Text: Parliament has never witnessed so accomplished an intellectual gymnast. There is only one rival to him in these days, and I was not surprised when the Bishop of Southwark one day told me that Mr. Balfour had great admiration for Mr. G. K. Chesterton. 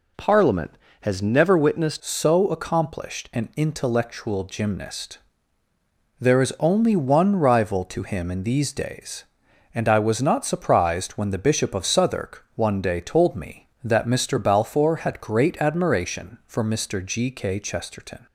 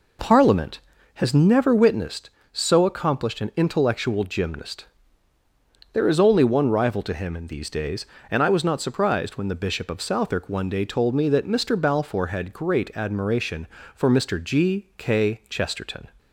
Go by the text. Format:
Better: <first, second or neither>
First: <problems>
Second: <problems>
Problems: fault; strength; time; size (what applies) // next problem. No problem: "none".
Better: second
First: changes voice at "so"; from 1.9 s on; 16.3 s long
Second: none